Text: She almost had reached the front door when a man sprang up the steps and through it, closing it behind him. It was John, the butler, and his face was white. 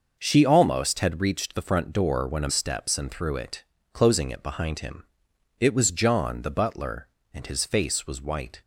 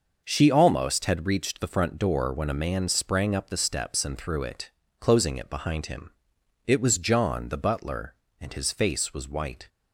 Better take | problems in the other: second | starts louder than the rest; noticeable; until 1.2 s; 6 dB; noticeable in the second // skips "man sprang up the"; at 2.5 s

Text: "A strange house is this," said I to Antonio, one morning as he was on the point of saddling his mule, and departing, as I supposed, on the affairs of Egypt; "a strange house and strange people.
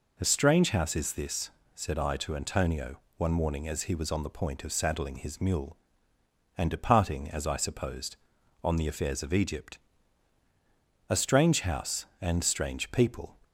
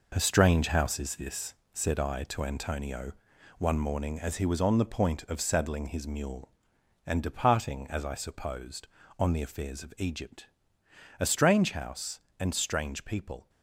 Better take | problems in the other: first | gets quieter; strong; throughout; 8 dB

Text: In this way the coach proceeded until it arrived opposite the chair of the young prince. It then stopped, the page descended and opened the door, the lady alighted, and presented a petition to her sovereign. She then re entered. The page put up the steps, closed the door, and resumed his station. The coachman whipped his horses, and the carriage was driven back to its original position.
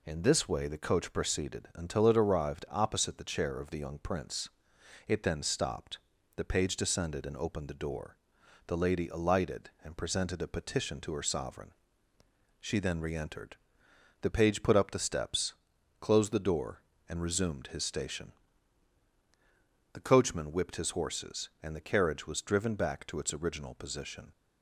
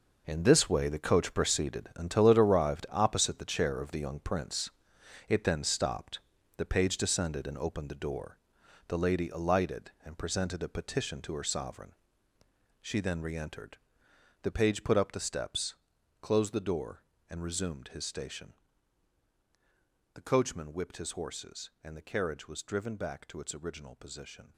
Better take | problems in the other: first | gets quieter; strong; throughout; 11.5 dB

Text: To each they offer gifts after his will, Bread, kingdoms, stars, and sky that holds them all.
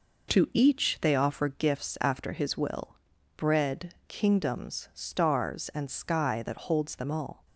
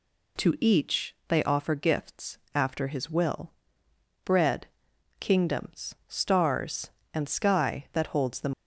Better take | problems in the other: first | pauses between "gifts" and "after"; slight; at 2.3 s; 0.18 s long // stops before "all"; at 8.5 s

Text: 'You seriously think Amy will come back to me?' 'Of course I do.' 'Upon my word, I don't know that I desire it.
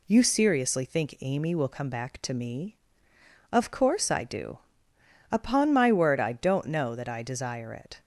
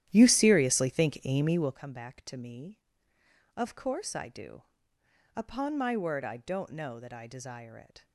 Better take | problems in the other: first | starts louder than the rest; strong; until 1.8 s; 12 dB

